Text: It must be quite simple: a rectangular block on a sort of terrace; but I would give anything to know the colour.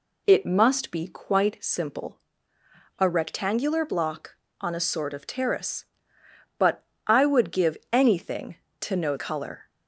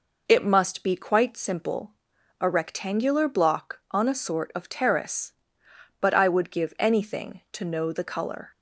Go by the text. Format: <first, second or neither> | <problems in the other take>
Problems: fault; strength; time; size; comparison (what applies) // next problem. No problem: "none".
second | pauses between "but" and "I"; slight; at 6.8 s; 0.24 s long // pauses between "give" and "anything"; slight; at 7.7 s; 0.16 s long // skips "the"; at 9.1 s